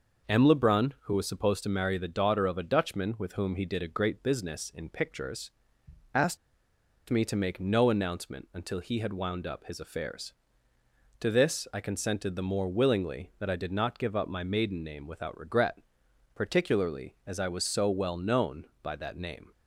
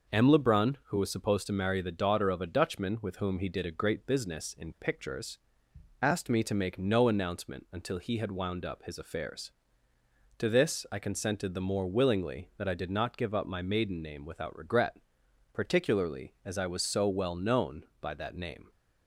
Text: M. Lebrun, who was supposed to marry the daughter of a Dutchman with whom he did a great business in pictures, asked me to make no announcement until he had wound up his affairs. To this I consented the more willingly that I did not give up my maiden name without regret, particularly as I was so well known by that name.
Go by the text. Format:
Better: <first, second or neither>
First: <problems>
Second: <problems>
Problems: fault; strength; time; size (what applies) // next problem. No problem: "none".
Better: second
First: pauses between "asked" and "me"; noticeable; at 6.3 s; 0.71 s long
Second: none